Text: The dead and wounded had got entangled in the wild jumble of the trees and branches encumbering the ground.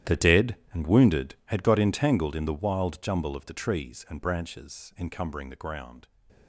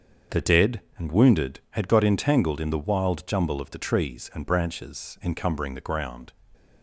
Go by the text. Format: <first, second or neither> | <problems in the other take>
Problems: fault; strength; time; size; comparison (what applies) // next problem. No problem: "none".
second | gets quieter; strong; throughout; 16 dB // starts louder than the rest; strong; until 1.2 s; 11.5 dB; also in the second